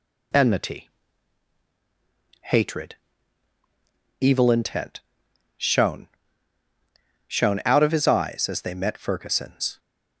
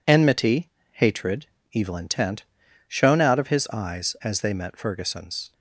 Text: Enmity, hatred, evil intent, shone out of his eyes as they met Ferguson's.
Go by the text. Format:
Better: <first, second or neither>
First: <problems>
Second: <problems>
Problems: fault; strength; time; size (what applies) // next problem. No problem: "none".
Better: second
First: says "shone" twice; at 7.2 s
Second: none